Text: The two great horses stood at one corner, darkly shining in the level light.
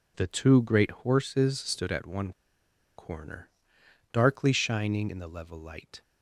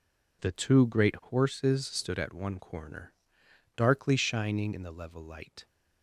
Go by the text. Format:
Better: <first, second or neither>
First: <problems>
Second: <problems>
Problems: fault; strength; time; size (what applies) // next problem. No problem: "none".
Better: second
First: pauses between "one" and "corner"; noticeable; at 2.3 s; 0.66 s long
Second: none